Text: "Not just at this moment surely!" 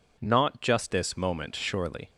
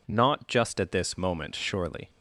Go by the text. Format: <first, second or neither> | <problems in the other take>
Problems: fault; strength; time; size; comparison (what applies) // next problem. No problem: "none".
second | skips "at"; at 0.9 s